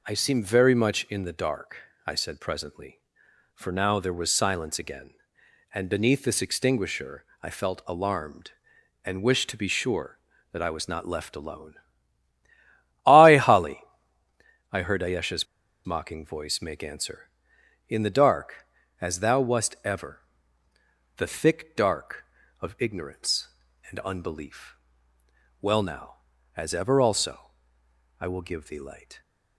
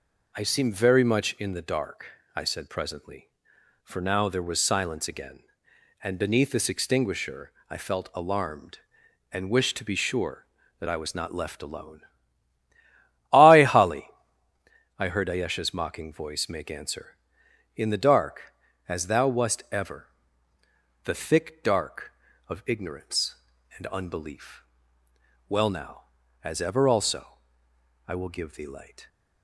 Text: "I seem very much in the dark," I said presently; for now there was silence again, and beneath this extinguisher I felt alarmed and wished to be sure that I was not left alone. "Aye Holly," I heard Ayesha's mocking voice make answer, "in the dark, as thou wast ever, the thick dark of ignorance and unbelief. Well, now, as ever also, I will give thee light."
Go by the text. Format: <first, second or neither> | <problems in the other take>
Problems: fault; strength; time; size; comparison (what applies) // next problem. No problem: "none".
second | pauses between "extinguisher" and "I"; slight; at 7.2 s; 0.18 s long; slight in the second // pauses between "Ayesha's" and "mocking"; at 15.4 s; 0.41 s long